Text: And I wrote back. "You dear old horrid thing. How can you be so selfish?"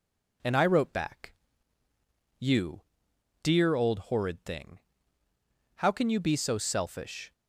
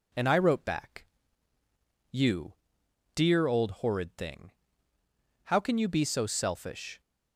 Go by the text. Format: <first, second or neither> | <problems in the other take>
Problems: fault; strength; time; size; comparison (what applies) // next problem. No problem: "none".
neither | pauses between "You" and "dear"; noticeable; the same in both